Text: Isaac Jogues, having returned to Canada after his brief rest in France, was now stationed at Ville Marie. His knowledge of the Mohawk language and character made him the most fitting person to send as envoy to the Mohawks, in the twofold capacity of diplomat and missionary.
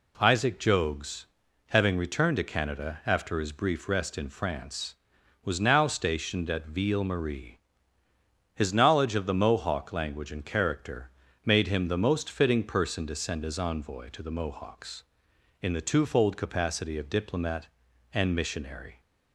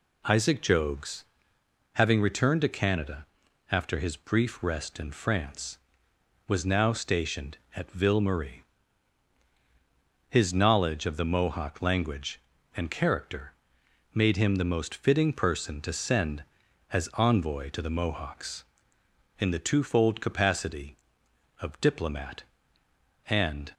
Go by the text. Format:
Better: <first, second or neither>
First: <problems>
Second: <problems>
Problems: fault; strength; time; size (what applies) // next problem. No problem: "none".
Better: first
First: pauses between "character" and "made"; slight; at 11.0 s; 0.34 s long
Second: pauses between "Canada" and "after"; noticeable; at 3.2 s; 0.46 s long // pauses between "character" and "made"; noticeable; at 13.5 s; 0.60 s long // stops before "missionary"; at 23.7 s